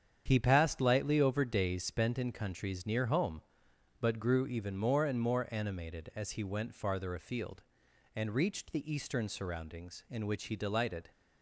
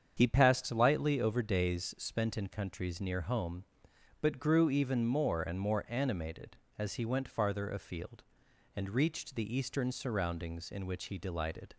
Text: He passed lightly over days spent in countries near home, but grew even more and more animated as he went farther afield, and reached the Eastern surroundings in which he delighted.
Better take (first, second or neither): neither